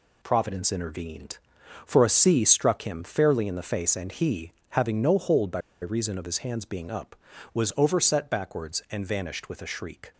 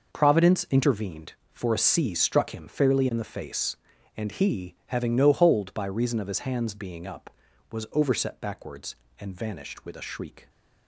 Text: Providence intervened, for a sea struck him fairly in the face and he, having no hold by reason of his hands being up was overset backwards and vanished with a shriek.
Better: second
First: pauses between "by" and "reason"; slight; at 5.5 s; 0.21 s long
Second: none

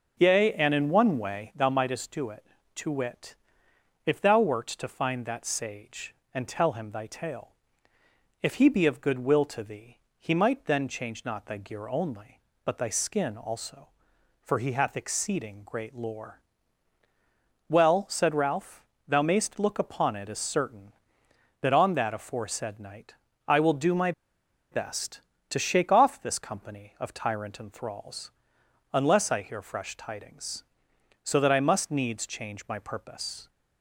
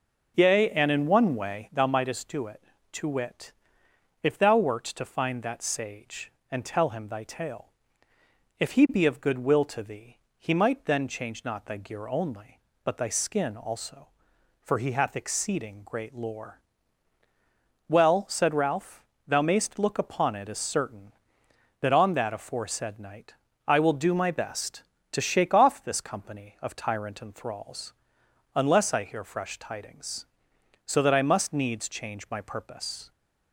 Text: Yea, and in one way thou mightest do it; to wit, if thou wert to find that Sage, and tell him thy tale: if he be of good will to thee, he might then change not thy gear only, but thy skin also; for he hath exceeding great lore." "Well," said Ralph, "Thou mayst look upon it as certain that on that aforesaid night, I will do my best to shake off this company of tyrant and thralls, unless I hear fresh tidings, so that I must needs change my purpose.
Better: second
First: pauses between "my" and "best"; noticeable; at 24.1 s; 0.60 s long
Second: none

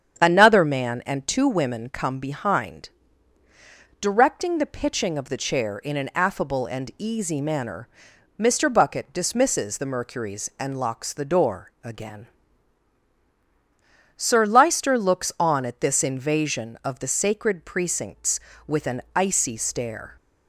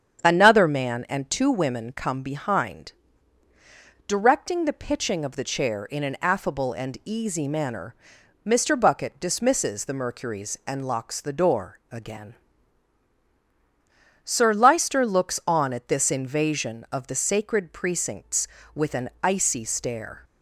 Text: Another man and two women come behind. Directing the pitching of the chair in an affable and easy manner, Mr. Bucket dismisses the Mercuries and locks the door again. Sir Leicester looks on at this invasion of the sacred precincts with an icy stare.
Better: neither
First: starts louder than the rest; strong; until 1.2 s; 8 dB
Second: starts louder than the rest; strong; until 1.2 s; 8 dB

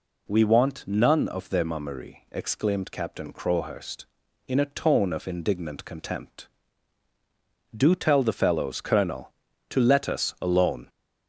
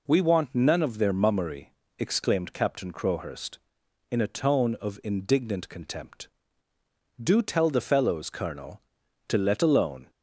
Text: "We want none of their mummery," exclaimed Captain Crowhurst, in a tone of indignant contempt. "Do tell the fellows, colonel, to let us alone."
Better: first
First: none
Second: skips "us"; at 9.6 s

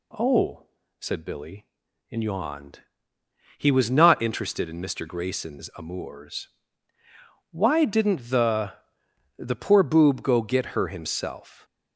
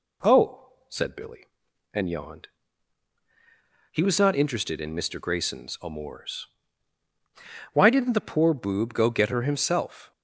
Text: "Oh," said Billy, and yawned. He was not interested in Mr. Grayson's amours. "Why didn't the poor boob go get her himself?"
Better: second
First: says "the" twice; at 9.3 s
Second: none

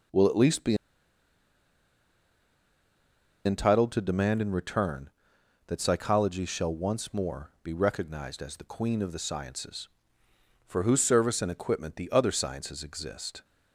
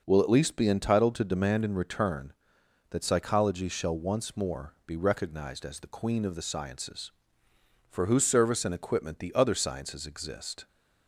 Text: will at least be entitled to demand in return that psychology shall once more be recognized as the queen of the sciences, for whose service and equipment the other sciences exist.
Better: second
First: pauses between "be" and "entitled"; strong; at 0.7 s; 2.6 s long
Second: none

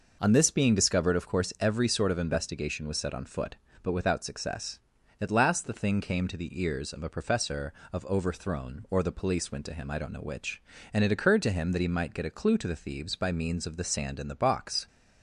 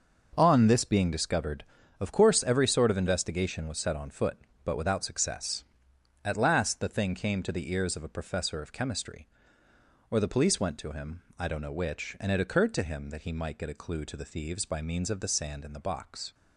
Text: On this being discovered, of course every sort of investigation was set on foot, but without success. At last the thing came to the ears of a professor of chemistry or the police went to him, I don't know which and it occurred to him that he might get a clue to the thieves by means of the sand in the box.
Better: second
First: says "overthrown" for "chemistry"; at 8.0 s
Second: none

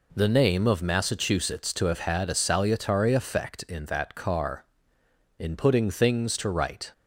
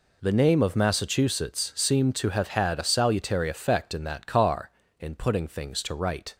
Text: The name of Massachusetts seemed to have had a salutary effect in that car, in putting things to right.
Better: second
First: skips "seemed"; at 1.7 s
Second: none

